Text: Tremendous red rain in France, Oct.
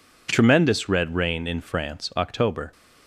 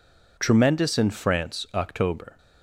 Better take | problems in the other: first | skips "red rain"; at 0.9 s

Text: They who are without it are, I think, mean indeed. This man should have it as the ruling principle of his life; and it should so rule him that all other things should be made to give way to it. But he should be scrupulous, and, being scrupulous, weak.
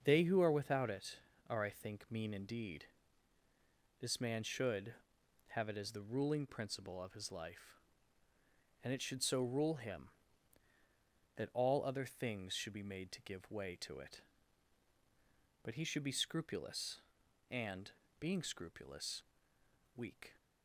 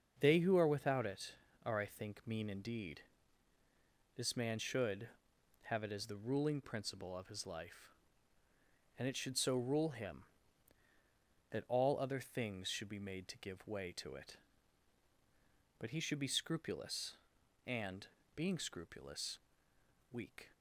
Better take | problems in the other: neither | starts louder than the rest; the same in both

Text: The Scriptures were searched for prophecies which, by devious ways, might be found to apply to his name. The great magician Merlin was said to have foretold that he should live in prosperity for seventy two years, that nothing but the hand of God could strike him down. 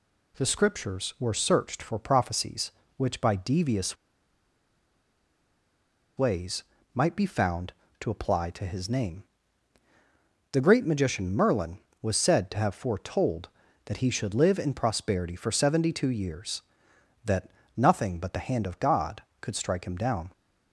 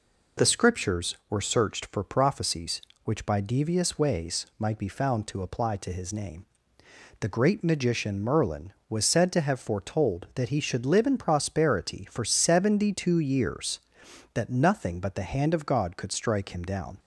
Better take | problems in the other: second | pauses between "devious" and "ways"; strong; at 3.9 s; 2.2 s long // pauses between "that" and "nothing"; slight; at 17.4 s; 0.26 s long

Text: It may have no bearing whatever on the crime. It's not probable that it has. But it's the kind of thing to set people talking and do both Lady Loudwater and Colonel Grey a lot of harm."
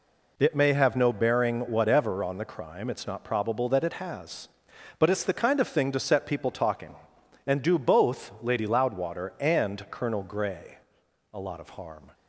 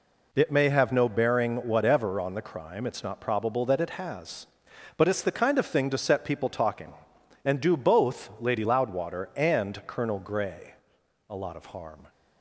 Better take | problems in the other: neither | pauses between "Grey" and "a"; noticeable; the same in both

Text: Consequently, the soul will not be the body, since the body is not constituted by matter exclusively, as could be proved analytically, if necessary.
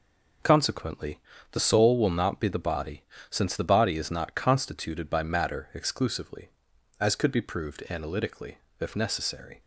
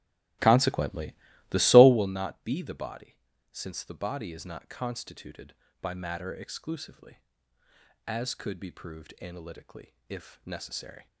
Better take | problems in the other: first | starts louder than the rest; strong; until 2.1 s; 14.5 dB

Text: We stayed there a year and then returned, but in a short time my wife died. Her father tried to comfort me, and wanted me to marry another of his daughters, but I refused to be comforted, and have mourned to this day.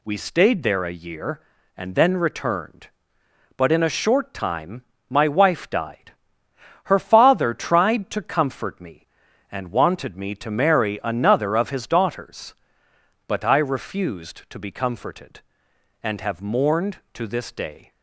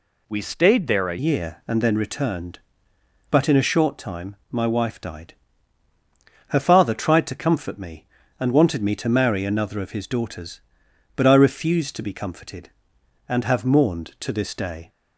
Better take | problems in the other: first | changes voice at "year"; from 1.1 s on; 13.7 s long // pauses between "time" and "my"; slight; at 4.3 s; 0.16 s long; slight in the first

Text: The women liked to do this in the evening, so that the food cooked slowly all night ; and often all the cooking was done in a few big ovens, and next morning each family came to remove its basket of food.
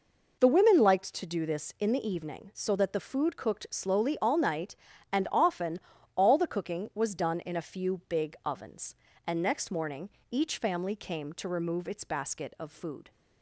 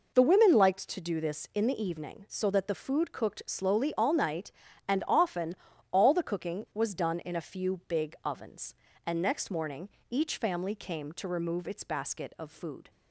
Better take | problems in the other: neither | pauses between "often" and "all"; the same in both // pauses between "morning" and "each"; slight; the same in both

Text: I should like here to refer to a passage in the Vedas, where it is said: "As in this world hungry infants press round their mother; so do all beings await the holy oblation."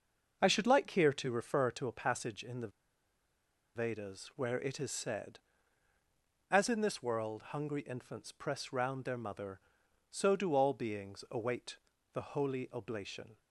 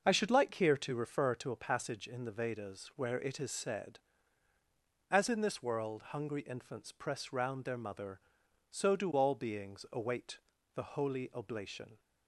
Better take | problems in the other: second | starts louder than the rest; until 1.4 s; 6 dB; also in the second // pauses between "the" and "Vedas"; at 2.6 s; 1.0 s long // pauses between "await" and "the"; slight; at 11.7 s; 0.34 s long; slight in the second

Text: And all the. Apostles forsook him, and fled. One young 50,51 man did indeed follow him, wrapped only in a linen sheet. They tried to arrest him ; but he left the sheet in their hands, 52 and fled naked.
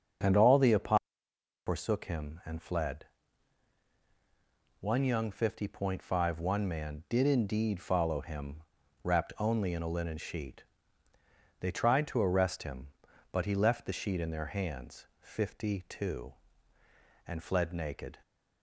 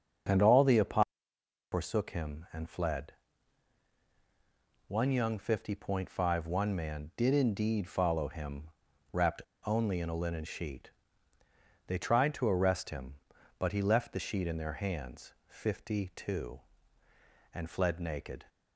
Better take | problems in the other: first | starts louder than the rest; until 1.9 s; 6.5 dB; also in the first // pauses between "Apostles" and "forsook"; noticeable; at 1.0 s; 0.66 s long; noticeable in the first // pauses between "wrapped" and "only"; slight; at 9.4 s; 0.23 s long

